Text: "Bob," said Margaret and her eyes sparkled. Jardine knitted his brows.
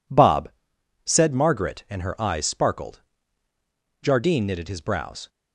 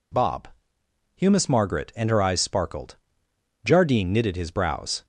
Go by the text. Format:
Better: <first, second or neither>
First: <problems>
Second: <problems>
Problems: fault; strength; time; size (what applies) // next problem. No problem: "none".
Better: first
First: none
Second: says "humus" for "said"; at 1.1 s